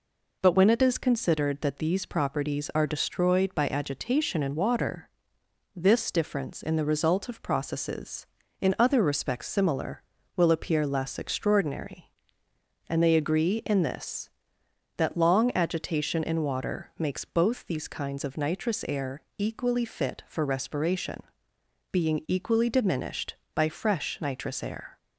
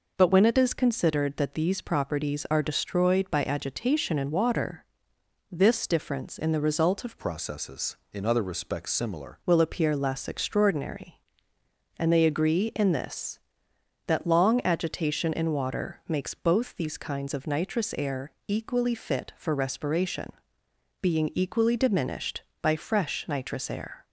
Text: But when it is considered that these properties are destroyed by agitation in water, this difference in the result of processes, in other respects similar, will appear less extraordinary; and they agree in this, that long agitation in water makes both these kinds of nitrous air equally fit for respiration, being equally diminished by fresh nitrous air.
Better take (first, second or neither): first